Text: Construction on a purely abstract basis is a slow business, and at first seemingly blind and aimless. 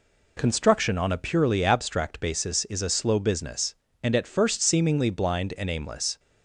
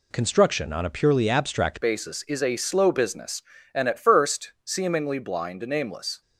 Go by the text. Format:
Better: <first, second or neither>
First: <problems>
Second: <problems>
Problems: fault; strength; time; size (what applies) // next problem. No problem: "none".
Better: first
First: none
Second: changes voice at "basis"; from 1.8 s on; 4.4 s long